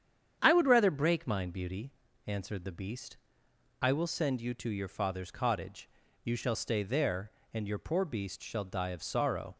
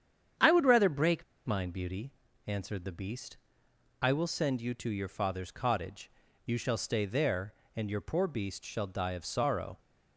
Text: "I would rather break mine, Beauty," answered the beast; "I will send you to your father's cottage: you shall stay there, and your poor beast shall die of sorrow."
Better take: first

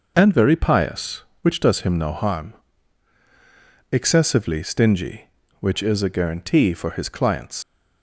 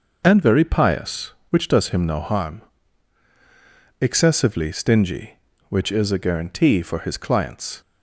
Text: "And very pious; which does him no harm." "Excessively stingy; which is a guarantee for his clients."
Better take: second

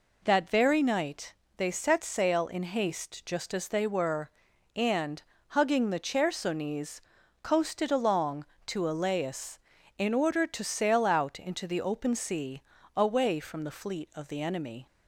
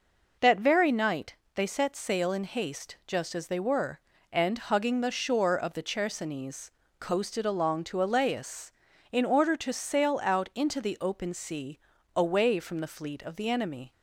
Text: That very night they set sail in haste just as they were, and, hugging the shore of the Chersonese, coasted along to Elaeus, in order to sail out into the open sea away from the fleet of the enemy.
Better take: second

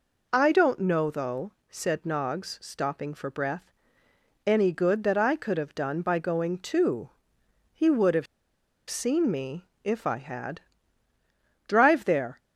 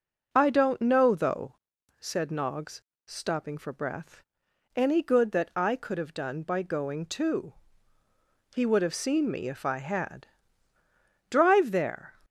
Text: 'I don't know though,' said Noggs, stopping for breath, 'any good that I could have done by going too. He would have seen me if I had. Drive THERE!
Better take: second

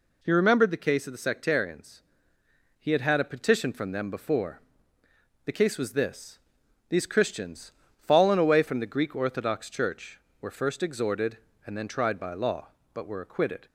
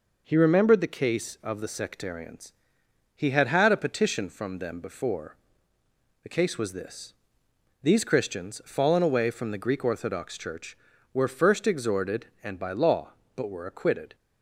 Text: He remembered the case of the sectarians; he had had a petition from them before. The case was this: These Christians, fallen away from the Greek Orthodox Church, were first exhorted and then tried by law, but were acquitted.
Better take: first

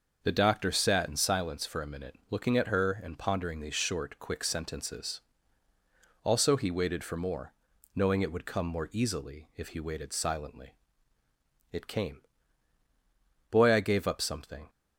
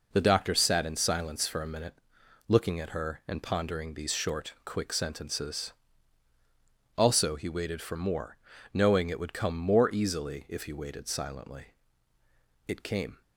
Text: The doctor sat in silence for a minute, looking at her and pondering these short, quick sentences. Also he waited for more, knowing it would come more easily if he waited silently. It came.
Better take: second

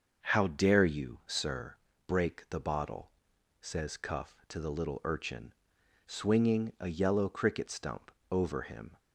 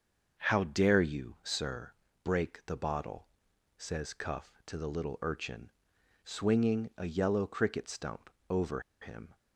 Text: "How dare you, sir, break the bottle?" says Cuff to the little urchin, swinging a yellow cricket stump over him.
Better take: first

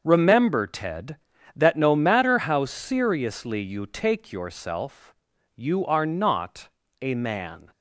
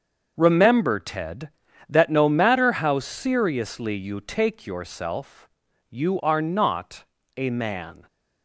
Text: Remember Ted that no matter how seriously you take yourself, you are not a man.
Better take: neither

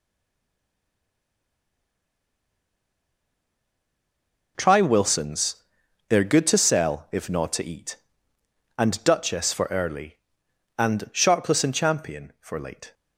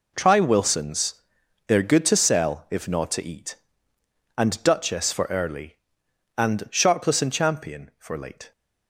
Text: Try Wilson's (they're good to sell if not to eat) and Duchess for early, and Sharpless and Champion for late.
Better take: second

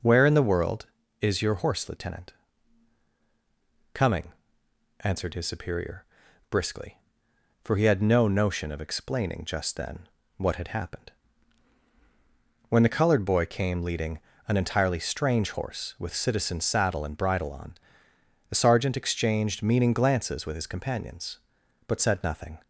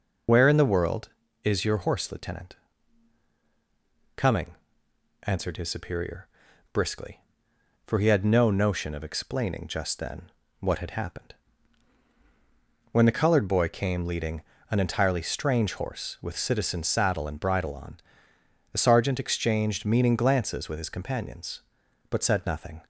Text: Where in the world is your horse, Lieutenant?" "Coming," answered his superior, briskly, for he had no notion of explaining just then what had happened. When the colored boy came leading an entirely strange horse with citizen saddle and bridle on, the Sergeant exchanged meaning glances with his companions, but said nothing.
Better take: first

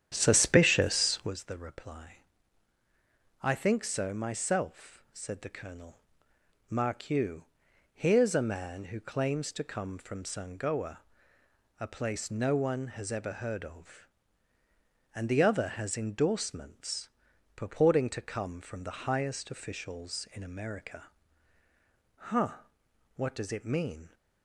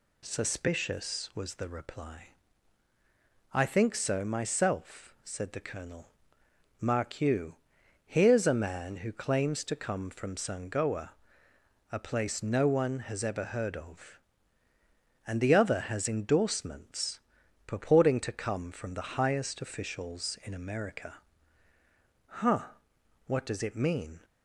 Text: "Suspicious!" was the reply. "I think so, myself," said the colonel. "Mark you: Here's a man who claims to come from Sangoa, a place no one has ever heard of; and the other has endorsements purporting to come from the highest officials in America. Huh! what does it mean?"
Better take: second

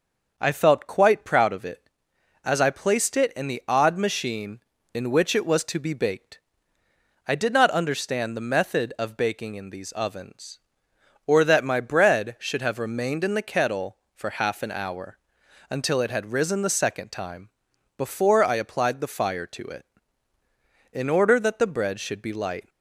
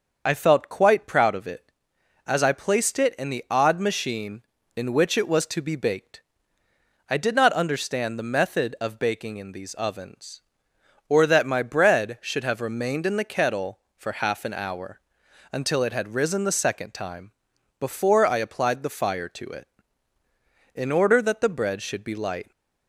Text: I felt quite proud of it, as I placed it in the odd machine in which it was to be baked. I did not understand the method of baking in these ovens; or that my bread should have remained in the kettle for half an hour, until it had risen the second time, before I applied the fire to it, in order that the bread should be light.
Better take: first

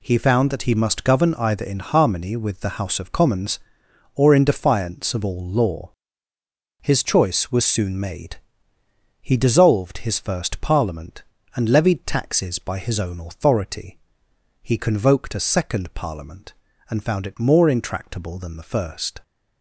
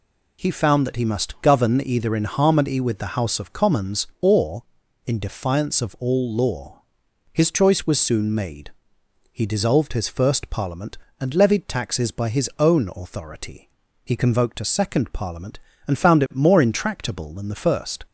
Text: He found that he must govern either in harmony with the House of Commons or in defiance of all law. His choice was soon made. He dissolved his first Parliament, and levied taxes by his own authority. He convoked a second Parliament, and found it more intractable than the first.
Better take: neither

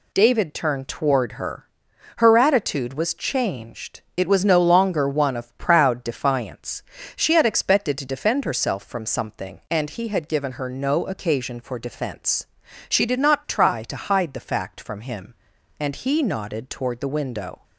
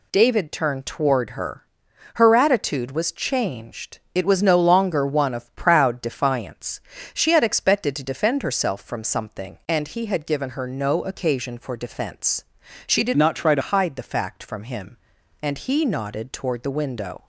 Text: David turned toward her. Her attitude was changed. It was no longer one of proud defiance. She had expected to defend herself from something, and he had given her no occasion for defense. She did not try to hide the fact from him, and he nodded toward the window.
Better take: first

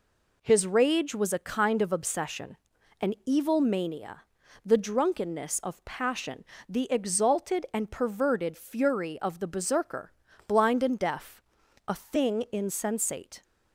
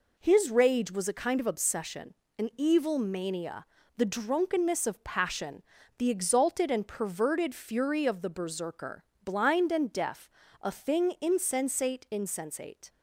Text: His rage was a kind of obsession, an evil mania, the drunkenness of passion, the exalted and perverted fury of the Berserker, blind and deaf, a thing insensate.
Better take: first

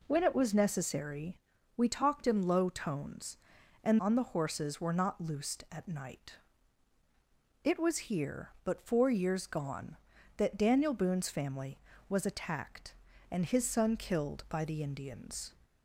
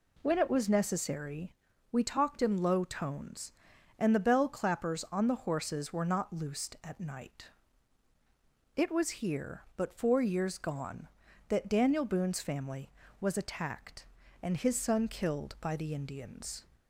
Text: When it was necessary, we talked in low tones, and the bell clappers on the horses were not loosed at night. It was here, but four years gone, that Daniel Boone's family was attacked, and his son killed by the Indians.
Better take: second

